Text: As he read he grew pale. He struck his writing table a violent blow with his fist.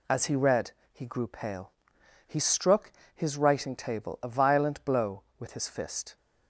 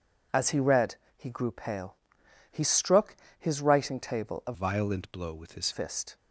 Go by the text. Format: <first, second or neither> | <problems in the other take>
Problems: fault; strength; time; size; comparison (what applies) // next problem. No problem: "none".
first | pauses between "read" and "he"; slight; at 0.9 s; 0.20 s long; slight in the first // pauses between "struck" and "his"; slight; at 3.1 s; 0.24 s long; slight in the first // changes voice from "violent" to "his"; from 4.5 to 5.7 s; 1.2 s long